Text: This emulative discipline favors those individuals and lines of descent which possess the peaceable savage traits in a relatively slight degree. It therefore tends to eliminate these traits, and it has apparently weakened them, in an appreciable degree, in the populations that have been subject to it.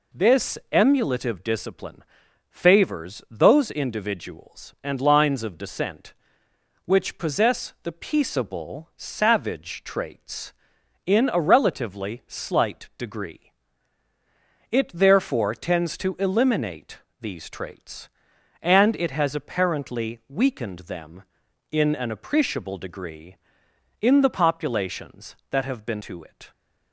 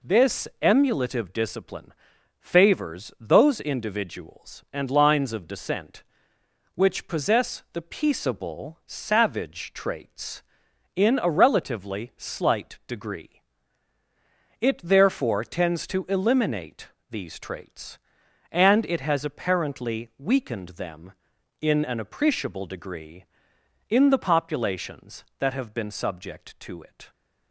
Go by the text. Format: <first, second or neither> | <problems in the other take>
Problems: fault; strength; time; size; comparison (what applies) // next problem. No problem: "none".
second | pauses between "discipline" and "favors"; noticeable; at 2.0 s; 0.46 s long; noticeable in the second // pauses between "eliminate" and "these"; slight; at 16.9 s; 0.22 s long; slight in the second // skips "subject"; at 26.0 s